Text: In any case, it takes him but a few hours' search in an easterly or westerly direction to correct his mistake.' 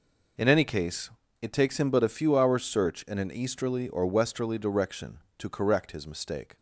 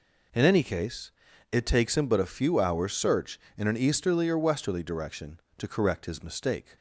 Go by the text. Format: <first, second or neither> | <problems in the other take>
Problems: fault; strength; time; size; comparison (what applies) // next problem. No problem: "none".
neither | none